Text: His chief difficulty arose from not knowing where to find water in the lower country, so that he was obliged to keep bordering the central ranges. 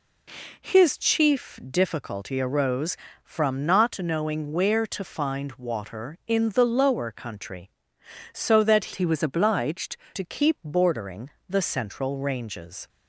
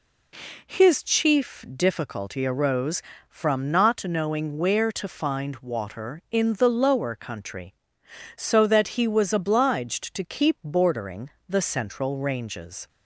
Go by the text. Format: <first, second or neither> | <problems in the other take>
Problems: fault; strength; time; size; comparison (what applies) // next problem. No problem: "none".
second | changes voice from "he" to "obliged"; from 8.9 to 9.9 s; 1.0 s long // pauses between "bordering" and "the"; slight; at 11.2 s; 0.22 s long; slight in the second